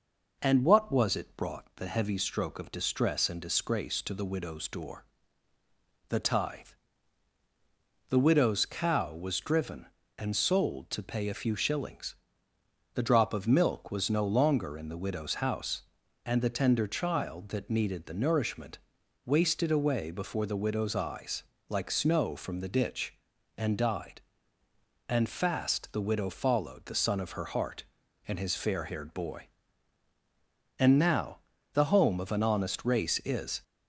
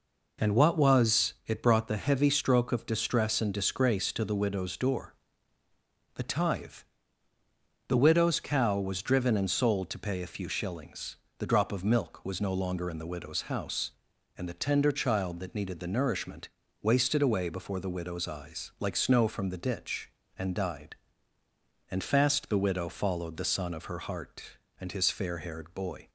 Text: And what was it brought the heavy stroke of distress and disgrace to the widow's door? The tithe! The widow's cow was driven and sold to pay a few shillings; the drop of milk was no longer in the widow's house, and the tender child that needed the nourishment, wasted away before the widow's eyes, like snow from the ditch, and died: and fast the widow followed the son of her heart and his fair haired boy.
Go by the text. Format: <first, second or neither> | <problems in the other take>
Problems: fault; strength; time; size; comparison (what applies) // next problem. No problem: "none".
second | goes on to say "And now the home of an honest race is"; strong; from 30.7 s on; 2.8 s long